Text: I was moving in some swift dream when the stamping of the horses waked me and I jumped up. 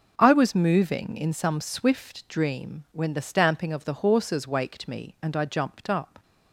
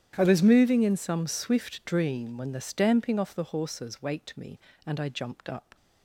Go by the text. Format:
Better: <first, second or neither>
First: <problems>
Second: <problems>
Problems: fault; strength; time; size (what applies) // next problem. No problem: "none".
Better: first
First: none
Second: starts louder than the rest; strong; until 1.1 s; 10 dB // says "off" for "of"; at 3.1 s